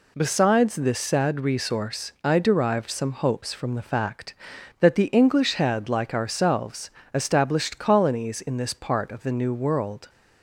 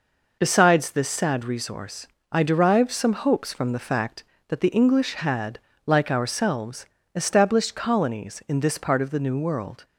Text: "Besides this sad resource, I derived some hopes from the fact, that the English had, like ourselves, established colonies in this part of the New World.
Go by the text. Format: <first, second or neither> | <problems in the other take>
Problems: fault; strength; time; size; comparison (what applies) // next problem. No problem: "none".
neither | none